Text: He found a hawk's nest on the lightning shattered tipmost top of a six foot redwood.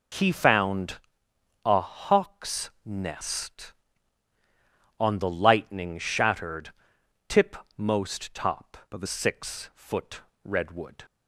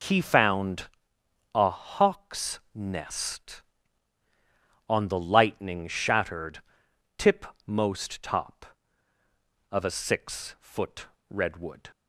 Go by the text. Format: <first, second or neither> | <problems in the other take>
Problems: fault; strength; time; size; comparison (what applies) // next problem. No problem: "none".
second | pauses between "found" and "a"; noticeable; at 0.9 s; 0.66 s long; noticeable in the second // pauses between "hawk's" and "nest"; slight; at 2.6 s; 0.16 s long; slight in the second // pauses between "shattered" and "tipmost"; noticeable; at 6.7 s; 0.58 s long; noticeable in the second // changes voice from "of" to "a"; from 8.9 to 9.0 s; 0.1 s long // pauses between "foot" and "redwood"; slight; at 10.2 s; 0.22 s long; slight in the second